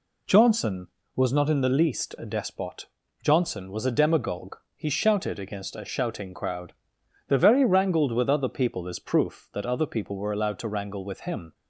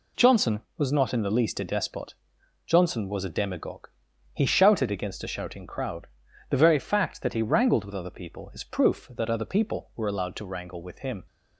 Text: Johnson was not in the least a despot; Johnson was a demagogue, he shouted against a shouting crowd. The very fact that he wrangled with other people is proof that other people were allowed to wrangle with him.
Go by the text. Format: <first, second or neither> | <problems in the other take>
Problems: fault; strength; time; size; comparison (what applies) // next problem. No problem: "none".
second | skips "fact that he"; at 7.6 s